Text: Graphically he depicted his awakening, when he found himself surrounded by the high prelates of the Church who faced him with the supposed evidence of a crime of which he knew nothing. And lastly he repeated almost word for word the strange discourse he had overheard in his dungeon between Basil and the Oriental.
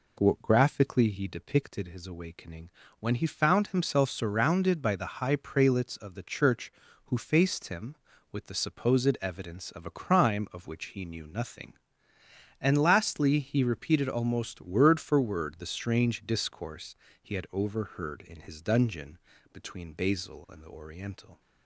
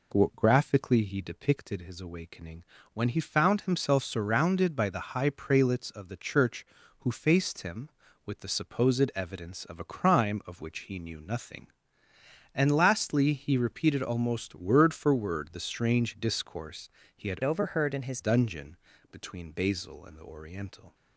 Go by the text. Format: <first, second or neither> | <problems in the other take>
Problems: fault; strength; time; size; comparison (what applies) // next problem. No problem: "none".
first | pauses between "discourse" and "he"; slight; at 16.8 s; 0.26 s long; slight in the first // changes voice from "overheard" to "his"; from 17.4 to 18.2 s; 0.8 s long // pauses between "dungeon" and "between"; slight; at 18.7 s; 0.34 s long; slight in the first